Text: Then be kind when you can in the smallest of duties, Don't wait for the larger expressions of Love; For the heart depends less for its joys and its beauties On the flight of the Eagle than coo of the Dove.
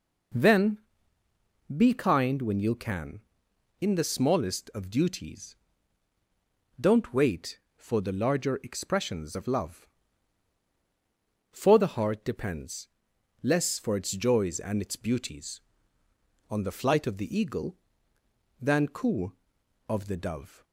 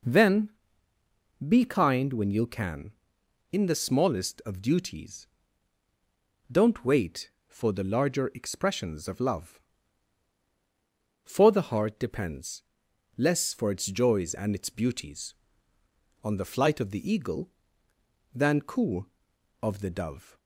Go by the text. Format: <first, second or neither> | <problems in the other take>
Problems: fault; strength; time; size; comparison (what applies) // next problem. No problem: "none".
neither | pauses between "Then" and "be"; noticeable; the same in both // pauses between "depends" and "less"; noticeable; the same in both